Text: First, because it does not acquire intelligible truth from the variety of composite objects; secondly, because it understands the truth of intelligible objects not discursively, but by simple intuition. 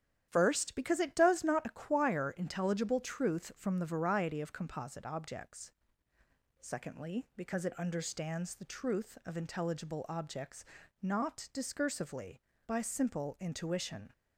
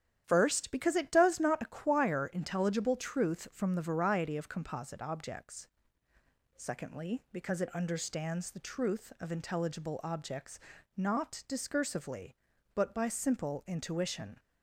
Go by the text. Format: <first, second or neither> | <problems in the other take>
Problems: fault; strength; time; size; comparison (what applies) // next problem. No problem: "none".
second | starts louder than the rest; strong; until 1.3 s; 10.5 dB; strong in the second // pauses between "objects" and "not"; slight; at 10.6 s; 0.36 s long; slight in the second // skips "but"; at 12.5 s